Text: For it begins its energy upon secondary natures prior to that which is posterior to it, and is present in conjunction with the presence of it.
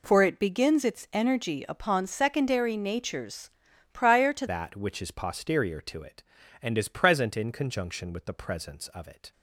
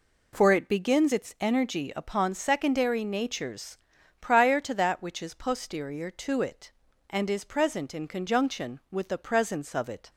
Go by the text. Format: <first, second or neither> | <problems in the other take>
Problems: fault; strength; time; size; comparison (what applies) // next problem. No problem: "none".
second | pauses between "natures" and "prior"; noticeable; at 3.4 s; 0.46 s long; noticeable in the second // changes voice at "that"; from 4.4 s on; 4.9 s long